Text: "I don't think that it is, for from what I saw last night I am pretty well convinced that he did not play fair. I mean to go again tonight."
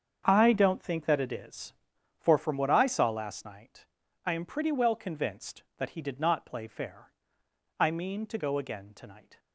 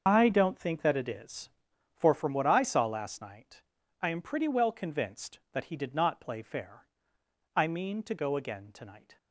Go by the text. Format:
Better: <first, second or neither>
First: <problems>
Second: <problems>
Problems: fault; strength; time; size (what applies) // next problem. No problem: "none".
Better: first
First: starts louder than the rest; strong; until 1.2 s; 7.5 dB // pauses between "night" and "I"; at 3.8 s; 0.40 s long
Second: loses the start of "I"; at 0.0 s; 65 ms // starts louder than the rest; until 1.0 s; 7 dB // pauses between "night" and "I"; at 3.6 s; 0.40 s long